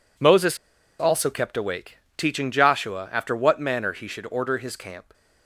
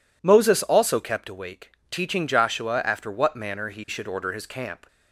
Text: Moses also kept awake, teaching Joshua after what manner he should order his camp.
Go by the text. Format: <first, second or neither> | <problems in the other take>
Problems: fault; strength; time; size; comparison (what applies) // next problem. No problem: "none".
second | pauses between "Moses" and "also"; at 0.5 s; 0.42 s long